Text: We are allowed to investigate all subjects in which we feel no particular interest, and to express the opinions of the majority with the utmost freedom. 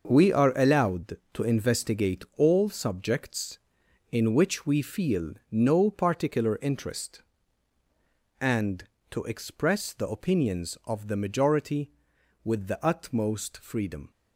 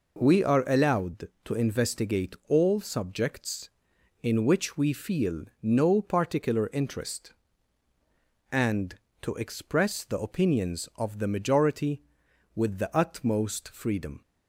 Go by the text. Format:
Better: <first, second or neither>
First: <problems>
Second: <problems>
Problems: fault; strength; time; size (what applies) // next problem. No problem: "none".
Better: second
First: gets quieter; strong; throughout; 10 dB // pauses between "feel" and "no"; slight; at 5.3 s; 0.16 s long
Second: pauses between "feel" and "no"; slight; at 5.4 s; 0.16 s long